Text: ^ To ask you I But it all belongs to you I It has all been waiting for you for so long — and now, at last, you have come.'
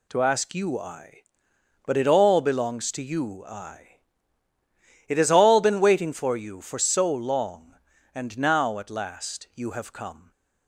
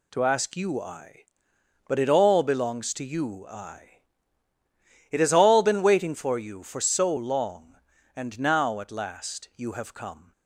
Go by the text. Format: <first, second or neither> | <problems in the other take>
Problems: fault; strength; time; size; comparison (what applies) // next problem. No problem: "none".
neither | pauses between "I" and "It"; the same in both